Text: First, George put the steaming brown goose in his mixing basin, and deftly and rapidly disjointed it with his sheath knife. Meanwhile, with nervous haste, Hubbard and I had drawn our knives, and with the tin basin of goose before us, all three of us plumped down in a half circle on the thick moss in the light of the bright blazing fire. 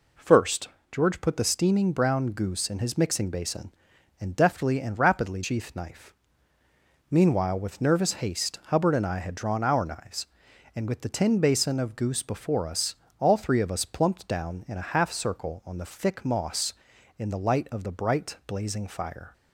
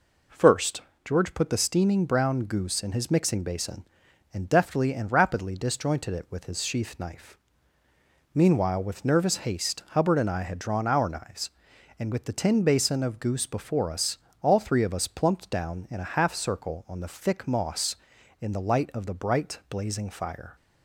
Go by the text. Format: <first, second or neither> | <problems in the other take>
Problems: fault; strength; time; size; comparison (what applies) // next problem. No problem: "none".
second | skips "disjointed it with his"; at 5.4 s